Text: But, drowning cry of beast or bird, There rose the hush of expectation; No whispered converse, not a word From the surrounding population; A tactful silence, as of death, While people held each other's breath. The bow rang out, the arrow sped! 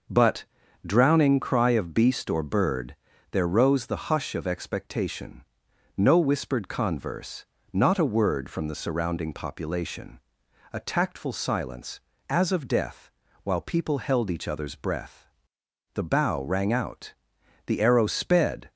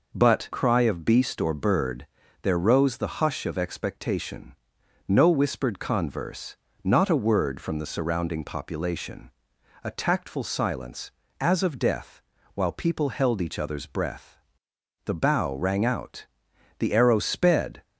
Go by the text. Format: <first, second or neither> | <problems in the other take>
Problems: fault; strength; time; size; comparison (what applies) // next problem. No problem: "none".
first | skips "drowning"; at 0.5 s